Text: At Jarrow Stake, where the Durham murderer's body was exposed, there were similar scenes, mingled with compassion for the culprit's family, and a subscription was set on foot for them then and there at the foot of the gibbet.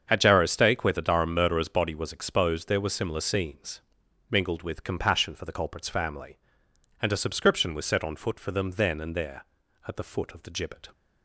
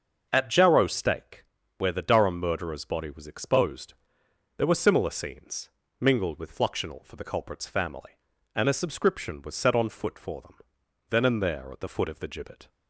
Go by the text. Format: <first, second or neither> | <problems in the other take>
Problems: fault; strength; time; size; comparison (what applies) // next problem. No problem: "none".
first | starts louder than the rest; until 1.3 s; 6.5 dB; strong in the first // says "fluxional" for "compassion"; at 6.5 s // pauses between "them" and "then"; noticeable; at 10.5 s; 0.54 s long